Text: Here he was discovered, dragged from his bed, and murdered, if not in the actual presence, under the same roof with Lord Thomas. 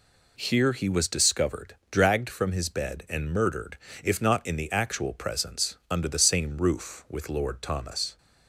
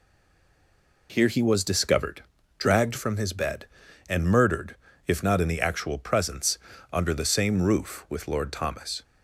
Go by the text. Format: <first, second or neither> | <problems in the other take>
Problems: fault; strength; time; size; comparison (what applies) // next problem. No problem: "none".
first | stays silent before the first word; until 1.0 s; 1.0 s long